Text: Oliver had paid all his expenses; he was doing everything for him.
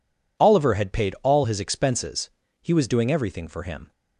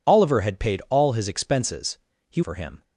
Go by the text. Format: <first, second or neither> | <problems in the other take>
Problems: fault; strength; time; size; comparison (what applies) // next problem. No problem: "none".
first | skips "was doing everything"; at 2.4 s